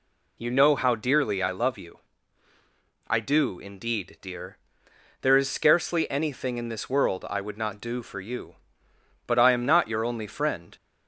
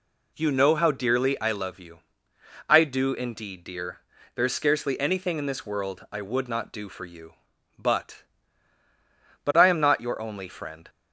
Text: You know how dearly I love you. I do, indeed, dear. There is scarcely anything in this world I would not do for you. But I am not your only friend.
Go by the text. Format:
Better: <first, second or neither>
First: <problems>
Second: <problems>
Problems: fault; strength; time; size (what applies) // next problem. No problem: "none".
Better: first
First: none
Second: says "But" twice; at 9.4 s